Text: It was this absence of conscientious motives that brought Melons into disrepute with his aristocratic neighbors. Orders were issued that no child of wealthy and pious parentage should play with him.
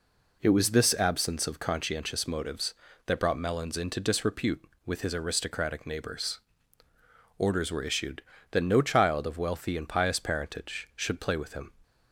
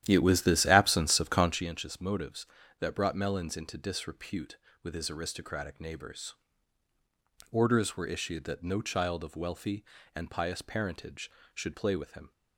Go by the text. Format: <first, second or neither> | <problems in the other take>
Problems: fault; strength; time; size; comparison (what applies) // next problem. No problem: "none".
first | starts louder than the rest; strong; until 1.7 s; 11.5 dB